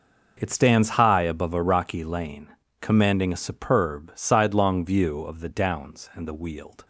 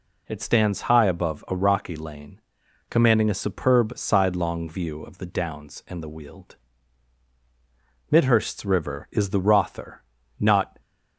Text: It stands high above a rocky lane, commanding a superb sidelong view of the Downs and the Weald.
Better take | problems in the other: first | goes on to say "Midhurst's river is the Rother not"; strong; from 8.1 s on; 2.7 s long

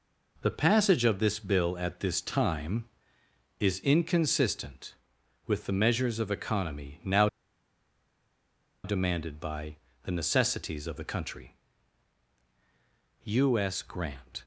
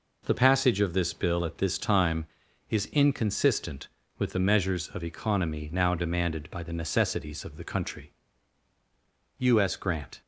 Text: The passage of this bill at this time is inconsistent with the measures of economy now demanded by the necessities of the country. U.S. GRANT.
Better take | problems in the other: second | pauses between "now" and "demanded"; strong; at 7.2 s; 1.5 s long // pauses between "by" and "the"; slight; at 9.7 s; 0.28 s long

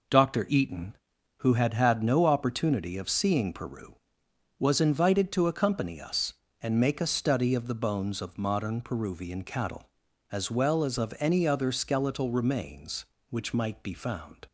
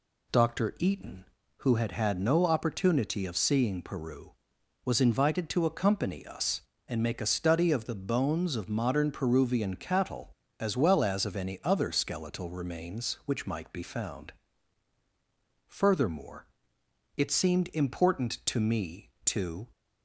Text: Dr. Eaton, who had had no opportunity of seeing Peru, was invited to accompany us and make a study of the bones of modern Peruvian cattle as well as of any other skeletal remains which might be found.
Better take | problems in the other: first | goes on to say "Furthermore it seemed important to me to"; strong; from 15.6 s on; 4.0 s long

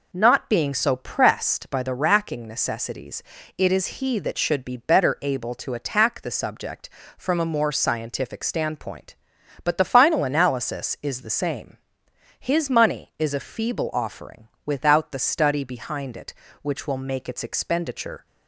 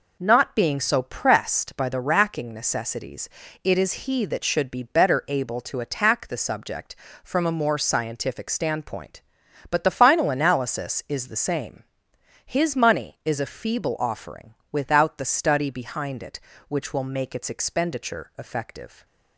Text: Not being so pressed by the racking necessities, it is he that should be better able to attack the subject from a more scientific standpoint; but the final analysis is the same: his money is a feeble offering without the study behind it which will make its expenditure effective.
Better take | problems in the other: second | pauses between "offering" and "without"; slight; at 14.4 s; 0.18 s long; slight in the second // stops before "effective"; at 18.2 s

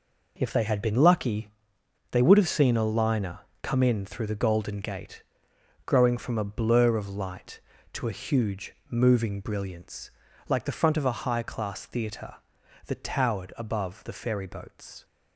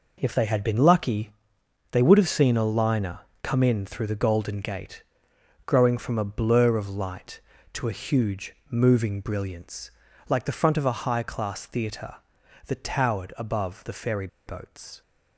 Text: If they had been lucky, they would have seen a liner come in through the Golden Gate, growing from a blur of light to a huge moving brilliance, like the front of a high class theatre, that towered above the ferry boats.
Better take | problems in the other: first | pauses between "liner" and "come"; slight; at 3.2 s; 0.20 s long; slight in the first // pauses between "huge" and "moving"; slight; at 8.5 s; 0.16 s long; slight in the first // pauses between "ferry" and "boats"; slight; at 14.2 s; 0.19 s long

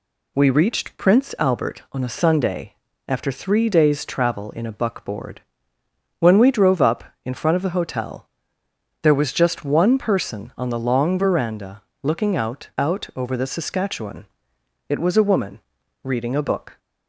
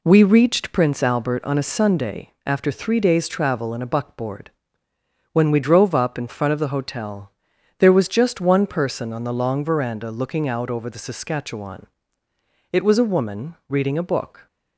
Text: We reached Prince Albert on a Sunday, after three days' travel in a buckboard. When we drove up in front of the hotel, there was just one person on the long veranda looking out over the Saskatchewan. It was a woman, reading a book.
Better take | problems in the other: second | pauses between "veranda" and "looking"; slight; at 11.8 s; 0.20 s long // says "out" twice; at 12.7 s

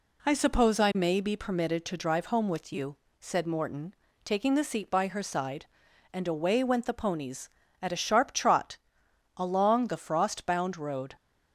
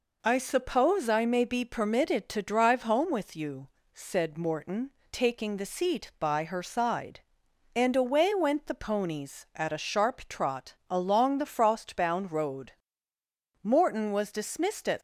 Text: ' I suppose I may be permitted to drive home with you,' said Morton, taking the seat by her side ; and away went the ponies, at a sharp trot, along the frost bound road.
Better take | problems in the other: first | goes on to say "Morton was dismissed at"; from 13.6 s on; 1.3 s long

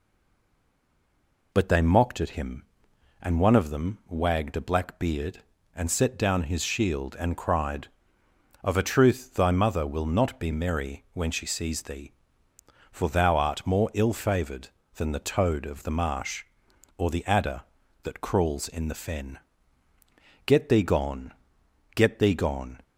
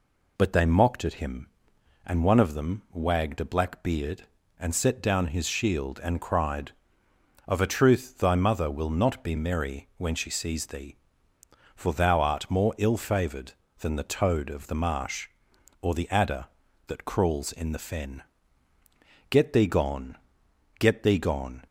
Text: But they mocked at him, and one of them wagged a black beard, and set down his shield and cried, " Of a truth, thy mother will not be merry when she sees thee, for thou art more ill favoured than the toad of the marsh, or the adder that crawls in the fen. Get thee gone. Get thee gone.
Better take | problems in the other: second | stays silent before the first word; noticeable; until 1.5 s; 1.5 s long

